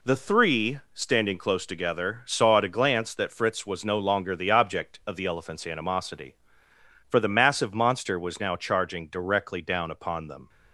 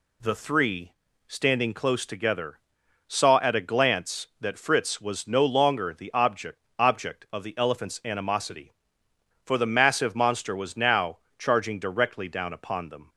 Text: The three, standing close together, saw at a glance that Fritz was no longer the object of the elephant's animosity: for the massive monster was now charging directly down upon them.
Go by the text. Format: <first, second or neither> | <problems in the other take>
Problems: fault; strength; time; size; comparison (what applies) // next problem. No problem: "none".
first | says "object" twice; at 6.7 s // pauses between "now" and "charging"; slight; at 11.1 s; 0.22 s long